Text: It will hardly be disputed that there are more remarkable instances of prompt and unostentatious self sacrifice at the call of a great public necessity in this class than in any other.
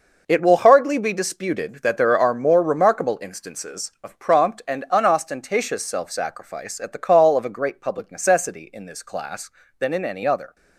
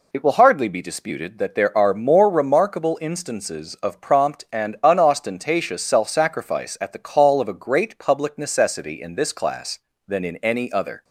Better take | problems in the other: second | gets quieter; strong; throughout; 9.5 dB

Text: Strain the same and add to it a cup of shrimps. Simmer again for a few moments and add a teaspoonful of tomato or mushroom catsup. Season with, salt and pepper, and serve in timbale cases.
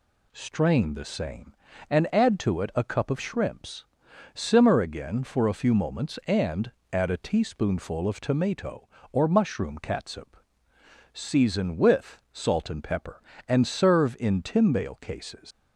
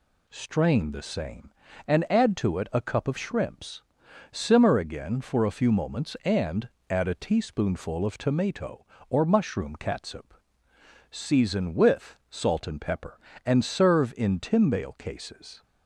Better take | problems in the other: second | pauses between "and" and "add"; slight; at 6.7 s; 0.20 s long; slight in the second // leaves "cases" unfinished; at 15.5 s; 145 ms

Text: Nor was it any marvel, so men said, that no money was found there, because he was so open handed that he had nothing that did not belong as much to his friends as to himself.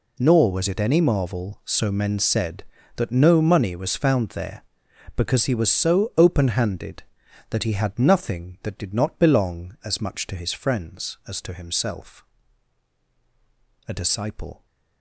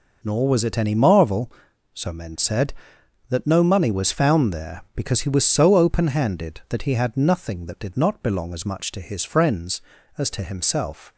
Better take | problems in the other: second | goes on to say "A disciple"; noticeable; from 13.8 s on; 0.78 s long

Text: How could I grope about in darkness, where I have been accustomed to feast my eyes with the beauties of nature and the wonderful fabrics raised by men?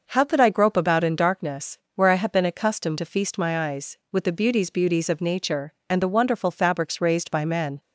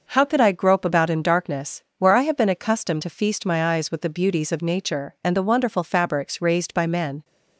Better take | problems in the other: second | says "beauties" twice; at 4.7 s

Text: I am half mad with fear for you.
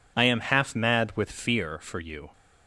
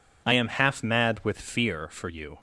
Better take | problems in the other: neither | none

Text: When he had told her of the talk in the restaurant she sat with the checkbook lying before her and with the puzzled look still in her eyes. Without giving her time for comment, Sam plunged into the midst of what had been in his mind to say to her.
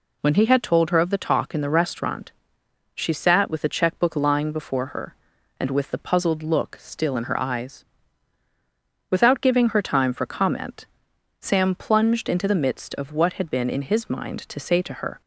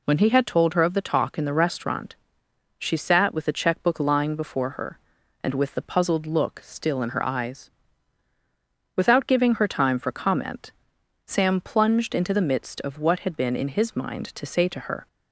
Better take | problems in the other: neither | pauses between "restaurant" and "she"; noticeable; the same in both

